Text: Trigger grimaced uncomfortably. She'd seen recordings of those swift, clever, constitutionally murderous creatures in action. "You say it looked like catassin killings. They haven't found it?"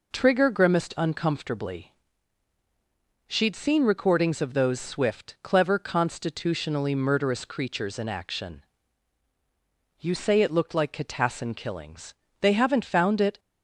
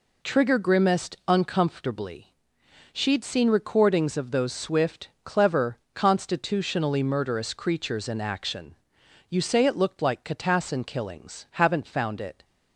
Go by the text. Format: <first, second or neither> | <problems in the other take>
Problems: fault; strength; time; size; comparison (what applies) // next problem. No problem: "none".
first | skips "They"; at 11.4 s